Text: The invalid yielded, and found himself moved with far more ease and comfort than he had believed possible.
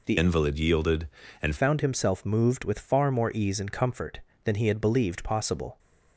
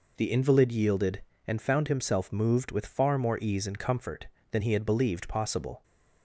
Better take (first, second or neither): second